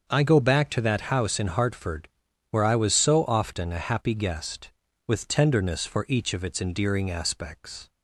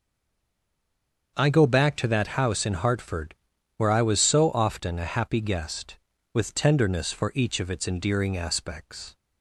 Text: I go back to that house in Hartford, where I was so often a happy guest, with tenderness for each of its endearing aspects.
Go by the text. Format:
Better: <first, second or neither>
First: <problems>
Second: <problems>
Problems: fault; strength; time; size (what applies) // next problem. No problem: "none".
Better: first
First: starts louder than the rest; until 1.0 s; 6.5 dB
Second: stays silent before the first word; noticeable; until 1.3 s; 1.3 s long // starts louder than the rest; until 2.3 s; 6.5 dB